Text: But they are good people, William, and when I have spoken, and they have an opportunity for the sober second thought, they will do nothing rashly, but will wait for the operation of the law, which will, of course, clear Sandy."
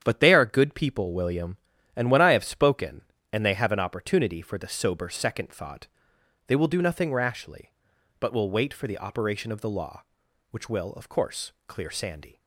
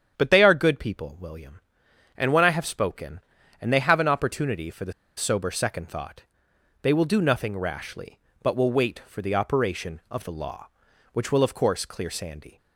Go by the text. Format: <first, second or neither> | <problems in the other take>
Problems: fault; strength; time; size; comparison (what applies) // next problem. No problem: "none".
first | starts louder than the rest; strong; until 1.1 s; 8.5 dB; strong in the first // pauses between "the" and "sober"; slight; at 4.9 s; 0.24 s long